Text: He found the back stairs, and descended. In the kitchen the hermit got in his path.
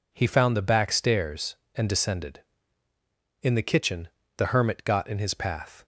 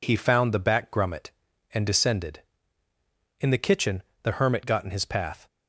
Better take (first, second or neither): first